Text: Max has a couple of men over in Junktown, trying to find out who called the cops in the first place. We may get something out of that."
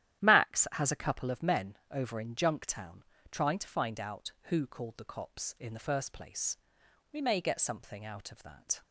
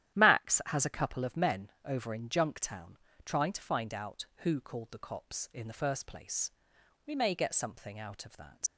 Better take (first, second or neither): first